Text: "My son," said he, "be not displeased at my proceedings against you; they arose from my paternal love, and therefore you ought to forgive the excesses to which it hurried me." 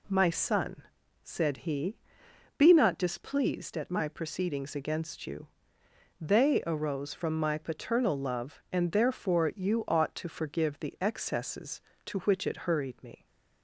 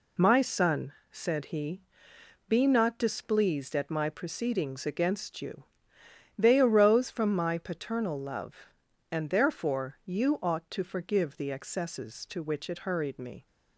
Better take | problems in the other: neither | none

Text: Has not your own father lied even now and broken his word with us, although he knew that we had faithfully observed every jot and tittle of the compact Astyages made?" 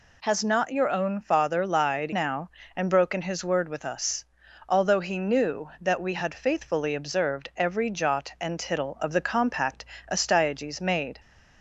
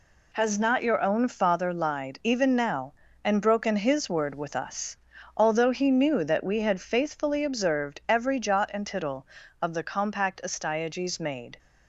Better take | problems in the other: second | skips "even"; at 2.1 s // pauses between "compact" and "Astyages"; slight; at 9.8 s; 0.26 s long

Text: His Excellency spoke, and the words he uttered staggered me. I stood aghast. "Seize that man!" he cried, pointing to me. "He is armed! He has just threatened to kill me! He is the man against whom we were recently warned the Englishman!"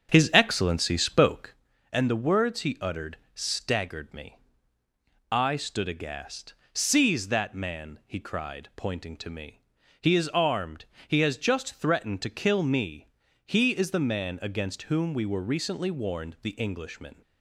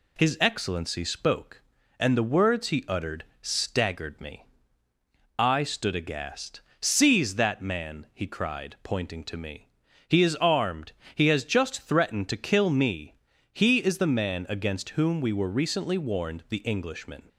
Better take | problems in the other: second | starts louder than the rest; strong; until 1.6 s; 7.5 dB // pauses between "uttered" and "staggered"; slight; at 3.1 s; 0.20 s long; slight in the second

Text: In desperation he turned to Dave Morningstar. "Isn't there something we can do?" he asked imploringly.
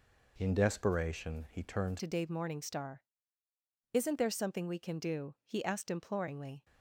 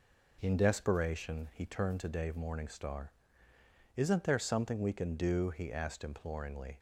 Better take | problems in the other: second | changes voice at "to"; from 1.9 s on; 4.7 s long

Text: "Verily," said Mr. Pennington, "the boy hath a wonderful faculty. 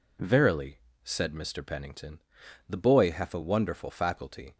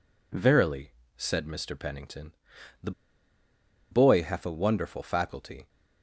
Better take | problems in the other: first | pauses between "the" and "boy"; at 2.9 s; 1.0 s long

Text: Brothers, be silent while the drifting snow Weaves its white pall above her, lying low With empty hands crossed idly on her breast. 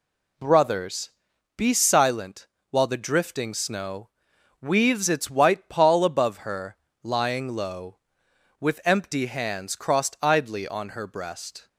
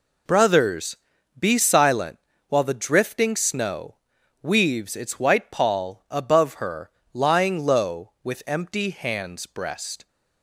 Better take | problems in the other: first | pauses between "silent" and "while"; slight; at 2.1 s; 0.30 s long; slight in the first // pauses between "snow" and "Weaves"; noticeable; at 3.9 s; 0.48 s long; noticeable in the first // skips "crossed idly on her"; at 9.4 s

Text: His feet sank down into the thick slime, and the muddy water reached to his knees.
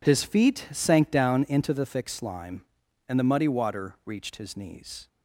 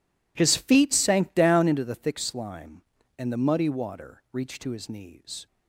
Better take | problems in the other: second | skips "to"; at 4.3 s

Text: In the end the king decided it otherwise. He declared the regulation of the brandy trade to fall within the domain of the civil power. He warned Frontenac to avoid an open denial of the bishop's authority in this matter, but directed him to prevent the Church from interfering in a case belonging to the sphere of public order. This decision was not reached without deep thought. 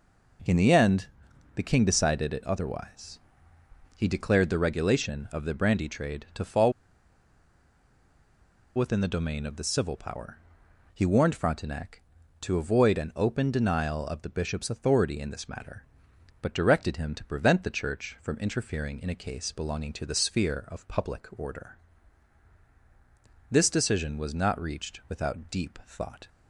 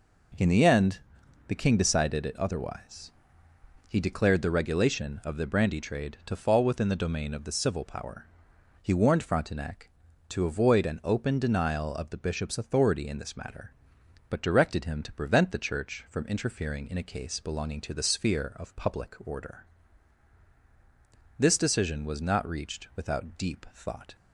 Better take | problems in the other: second | pauses between "end" and "the"; noticeable; at 1.0 s; 0.48 s long; noticeable in the second // pauses between "fall" and "within"; strong; at 6.7 s; 2.0 s long

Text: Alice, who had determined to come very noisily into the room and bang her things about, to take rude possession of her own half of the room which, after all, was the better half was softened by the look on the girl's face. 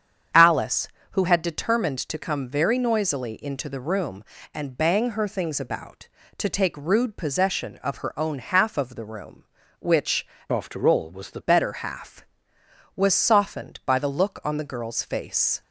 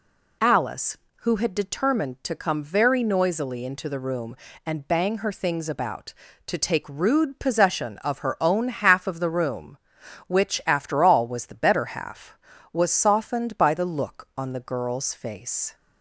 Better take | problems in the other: second | starts louder than the rest; strong; until 1.5 s; 8 dB // changes voice from "after" to "the"; from 10.5 to 11.3 s; 0.8 s long

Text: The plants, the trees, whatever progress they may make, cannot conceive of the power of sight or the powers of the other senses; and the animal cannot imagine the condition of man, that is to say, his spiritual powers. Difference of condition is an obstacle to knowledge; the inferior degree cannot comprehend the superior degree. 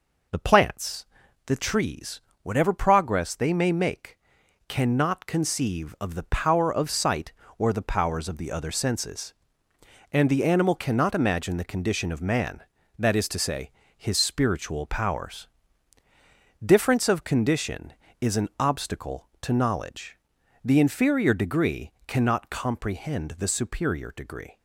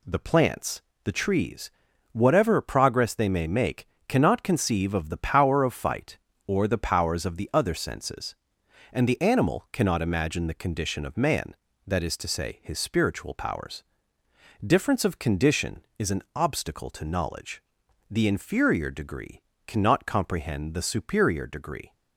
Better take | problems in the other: first | says "fight" for "sight"; at 5.7 s // pauses between "degree" and "cannot"; slight; at 19.4 s; 0.28 s long; slight in the first

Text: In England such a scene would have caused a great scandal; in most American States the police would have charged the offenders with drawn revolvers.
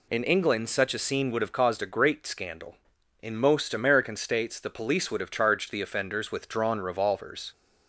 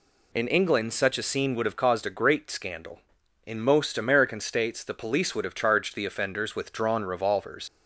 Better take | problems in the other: first | leaves "revolvers" unfinished; at 7.6 s; 80 ms

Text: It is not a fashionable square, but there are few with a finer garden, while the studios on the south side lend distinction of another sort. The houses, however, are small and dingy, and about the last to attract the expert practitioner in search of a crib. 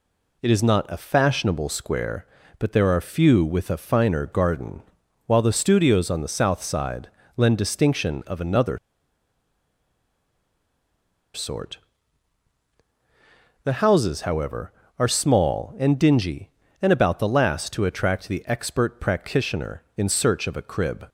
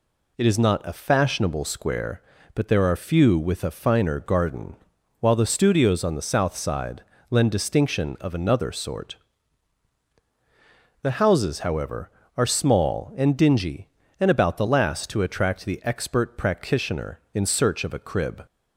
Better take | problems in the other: second | pauses between "side" and "lend"; slight; at 7.0 s; 0.28 s long; slight in the second // pauses between "another" and "sort"; strong; at 8.7 s; 2.5 s long

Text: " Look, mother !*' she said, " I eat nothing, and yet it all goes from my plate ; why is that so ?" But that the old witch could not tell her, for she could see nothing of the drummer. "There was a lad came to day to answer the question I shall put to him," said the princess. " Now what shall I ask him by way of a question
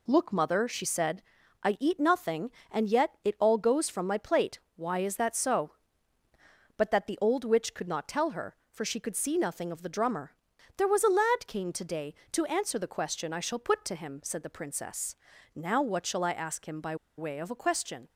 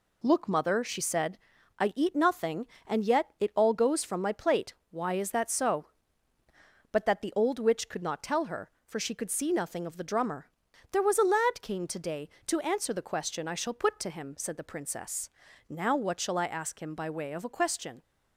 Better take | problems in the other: second | pauses between "by" and "way"; slight; at 16.9 s; 0.23 s long

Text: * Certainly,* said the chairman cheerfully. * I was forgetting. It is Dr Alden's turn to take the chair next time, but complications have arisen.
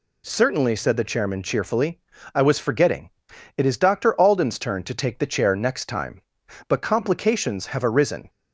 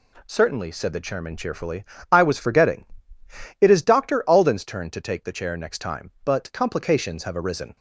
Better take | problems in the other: neither | none

